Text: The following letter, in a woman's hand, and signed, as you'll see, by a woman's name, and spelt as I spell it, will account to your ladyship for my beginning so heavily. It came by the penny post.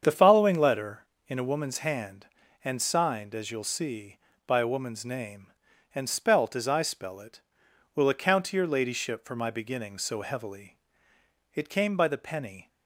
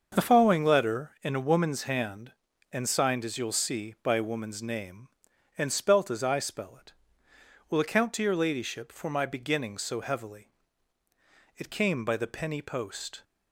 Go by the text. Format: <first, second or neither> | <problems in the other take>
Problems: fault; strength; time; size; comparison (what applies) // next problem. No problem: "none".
second | starts louder than the rest; strong; until 1.0 s; 7.5 dB; also in the second // stops before "post"; at 12.6 s